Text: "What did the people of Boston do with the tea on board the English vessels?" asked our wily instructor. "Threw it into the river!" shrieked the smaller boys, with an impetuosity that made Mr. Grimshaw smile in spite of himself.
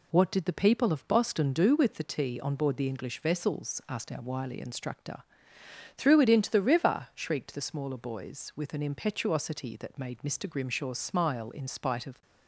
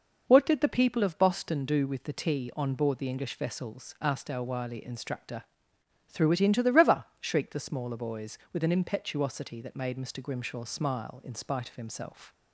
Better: second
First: stops before "himself"; at 12.2 s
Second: none

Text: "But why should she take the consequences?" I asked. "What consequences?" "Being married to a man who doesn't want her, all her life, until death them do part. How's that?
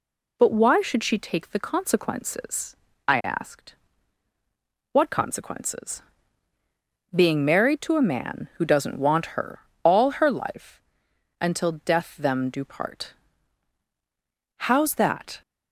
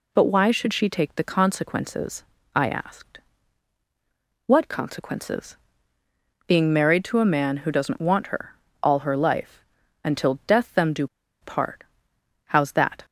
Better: first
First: none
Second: pauses between "do" and "part"; slight; at 11.0 s; 0.35 s long

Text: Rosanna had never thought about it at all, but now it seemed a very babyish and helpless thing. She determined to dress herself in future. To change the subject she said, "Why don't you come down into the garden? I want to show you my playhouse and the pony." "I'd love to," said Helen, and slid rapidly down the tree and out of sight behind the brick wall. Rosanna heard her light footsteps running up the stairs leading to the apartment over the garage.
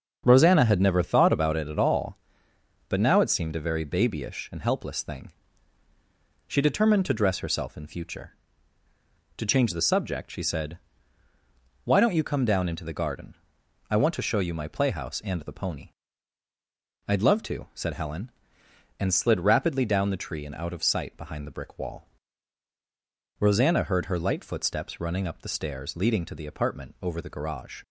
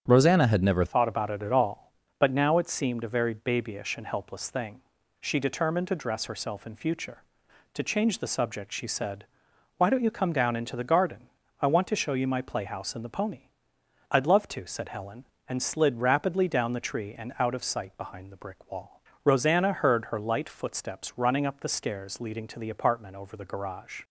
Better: first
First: starts louder than the rest; until 1.2 s; 7 dB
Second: starts louder than the rest; strong; until 1.0 s; 8.5 dB // changes voice at "thought"; from 0.8 s on; 23.2 s long

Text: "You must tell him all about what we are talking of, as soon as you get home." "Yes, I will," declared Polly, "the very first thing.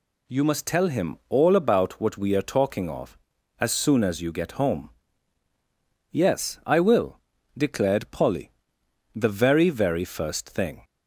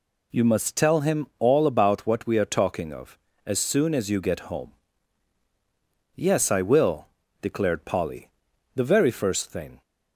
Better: second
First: says "very" twice; at 9.6 s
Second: none

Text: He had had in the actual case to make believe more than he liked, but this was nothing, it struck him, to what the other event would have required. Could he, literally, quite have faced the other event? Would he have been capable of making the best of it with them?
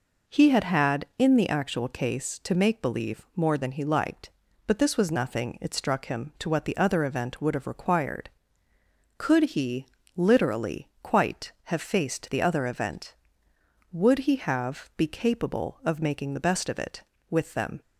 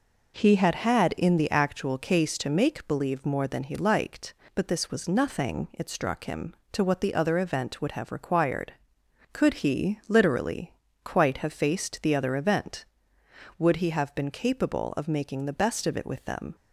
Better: second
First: says "be" for "been"; at 14.9 s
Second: none

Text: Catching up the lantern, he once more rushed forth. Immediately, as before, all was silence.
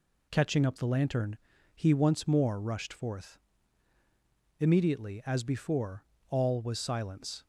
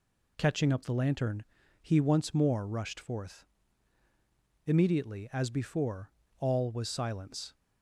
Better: neither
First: none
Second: none

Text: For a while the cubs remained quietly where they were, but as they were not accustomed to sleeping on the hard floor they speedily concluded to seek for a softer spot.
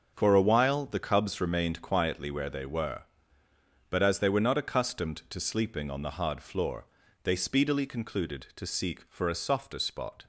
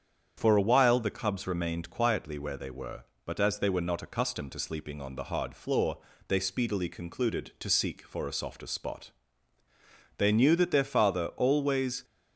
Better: first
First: starts louder than the rest; until 1.1 s; 6 dB // pauses between "floor" and "they"; at 6.8 s; 0.38 s long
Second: starts louder than the rest; strong; until 1.3 s; 8 dB // pauses between "floor" and "they"; slight; at 5.9 s; 0.30 s long // goes on to say "They knew that their father always"; strong; from 10.1 s on; 1.8 s long

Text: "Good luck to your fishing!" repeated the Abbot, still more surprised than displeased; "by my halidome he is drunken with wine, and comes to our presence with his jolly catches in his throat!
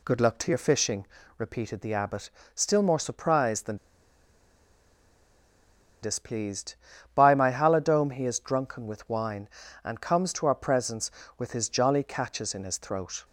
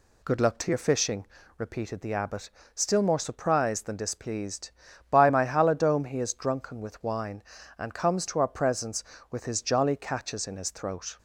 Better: second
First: pauses between "than" and "displeased"; strong; at 3.7 s; 2.2 s long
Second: none

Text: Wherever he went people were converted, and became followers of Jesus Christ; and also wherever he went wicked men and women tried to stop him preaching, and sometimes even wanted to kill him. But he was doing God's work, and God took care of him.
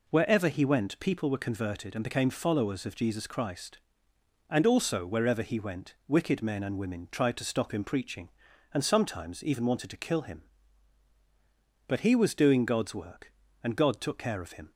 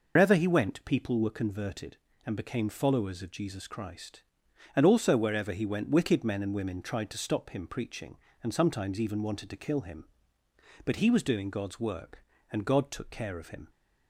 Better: first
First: none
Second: loses the start of "Wherever"; at 0.1 s; 115 ms

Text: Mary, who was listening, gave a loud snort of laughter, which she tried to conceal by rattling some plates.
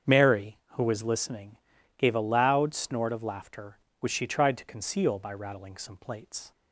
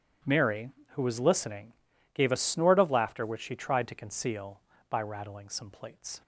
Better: first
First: starts louder than the rest; strong; until 1.2 s; 7.5 dB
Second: starts louder than the rest; strong; until 1.4 s; 9.5 dB // skips "loud"; at 2.3 s

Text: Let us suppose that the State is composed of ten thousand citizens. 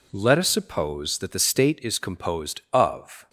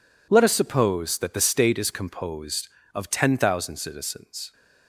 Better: second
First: stops before "ten thousand citizens"; at 3.2 s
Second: none

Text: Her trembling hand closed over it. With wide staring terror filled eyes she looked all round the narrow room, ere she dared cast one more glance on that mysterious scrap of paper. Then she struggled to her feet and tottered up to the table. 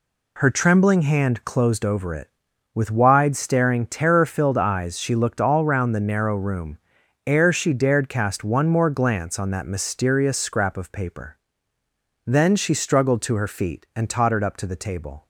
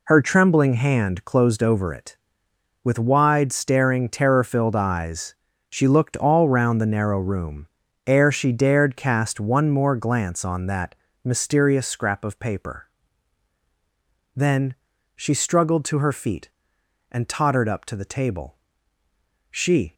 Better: first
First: none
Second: pauses between "eyes" and "she"; slight; at 5.3 s; 0.36 s long // pauses between "that" and "mysterious"; slight; at 10.9 s; 0.30 s long // pauses between "Then" and "she"; at 14.7 s; 0.42 s long // goes on to say "She"; slight; from 19.4 s on; 0.44 s long

